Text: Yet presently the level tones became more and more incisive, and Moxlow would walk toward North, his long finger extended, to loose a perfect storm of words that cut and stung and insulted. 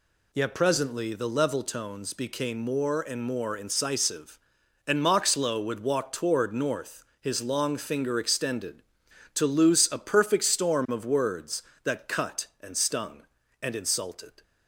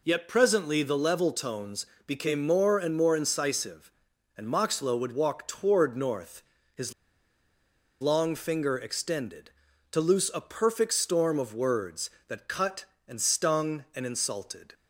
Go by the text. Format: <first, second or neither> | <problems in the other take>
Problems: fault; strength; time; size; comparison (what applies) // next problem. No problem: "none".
first | pauses between "tones" and "became"; slight; at 1.8 s; 0.20 s long // pauses between "his" and "long"; at 6.9 s; 1.0 s long